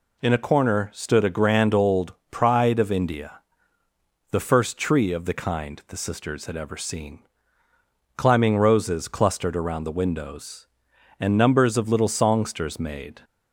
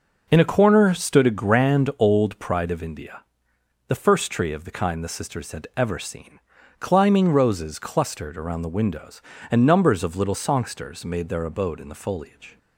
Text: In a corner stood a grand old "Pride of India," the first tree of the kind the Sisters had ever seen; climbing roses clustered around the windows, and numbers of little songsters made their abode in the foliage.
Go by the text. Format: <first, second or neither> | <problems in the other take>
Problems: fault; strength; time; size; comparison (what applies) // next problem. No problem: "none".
second | pauses between "old" and "Pride"; slight; at 2.1 s; 0.20 s long // stops before "their abode in the foliage"; at 13.2 s